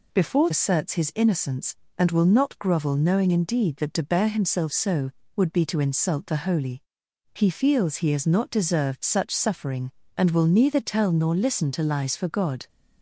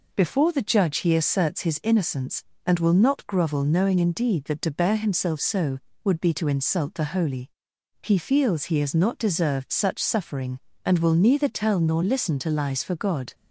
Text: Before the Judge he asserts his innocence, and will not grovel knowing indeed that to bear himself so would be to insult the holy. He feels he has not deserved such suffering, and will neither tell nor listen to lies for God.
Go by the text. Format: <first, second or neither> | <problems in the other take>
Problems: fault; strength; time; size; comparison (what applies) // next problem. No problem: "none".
second | skips "the Judge he"; at 0.4 s